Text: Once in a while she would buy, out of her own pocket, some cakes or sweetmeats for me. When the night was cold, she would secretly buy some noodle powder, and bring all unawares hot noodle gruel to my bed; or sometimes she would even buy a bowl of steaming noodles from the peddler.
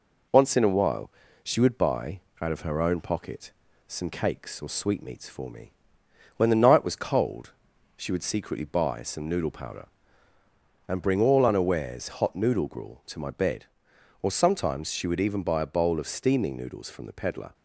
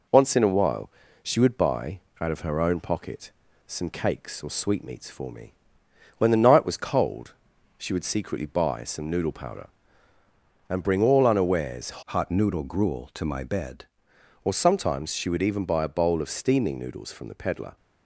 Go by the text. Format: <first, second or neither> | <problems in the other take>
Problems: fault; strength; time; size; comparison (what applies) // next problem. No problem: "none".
first | pauses between "while" and "she"; slight; at 0.8 s; 0.32 s long; slight in the first // changes voice from "hot" to "bed"; from 12.0 to 13.8 s; 1.8 s long